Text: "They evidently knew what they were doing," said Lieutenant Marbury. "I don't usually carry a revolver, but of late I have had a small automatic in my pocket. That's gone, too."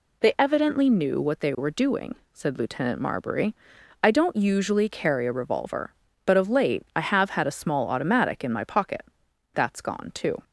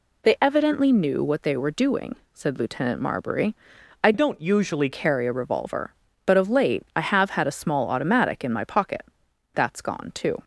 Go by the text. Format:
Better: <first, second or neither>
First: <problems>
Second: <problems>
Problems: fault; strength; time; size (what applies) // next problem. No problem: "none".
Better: first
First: none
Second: changes voice from "don't" to "usually"; from 4.1 to 4.9 s; 0.8 s long